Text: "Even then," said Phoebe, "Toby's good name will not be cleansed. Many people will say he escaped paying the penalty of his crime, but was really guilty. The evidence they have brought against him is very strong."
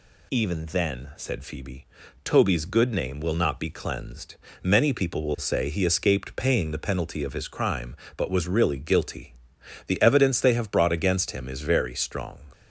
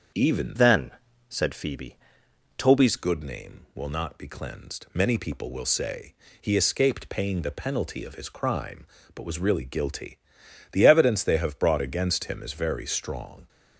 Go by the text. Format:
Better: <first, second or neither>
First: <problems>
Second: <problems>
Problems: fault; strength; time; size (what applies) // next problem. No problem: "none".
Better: first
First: none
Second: starts louder than the rest; until 1.5 s; 7 dB // changes voice from "then" to "Toby's"; from 0.5 to 2.9 s; 2.4 s long // pauses between "say" and "he"; slight; at 6.1 s; 0.26 s long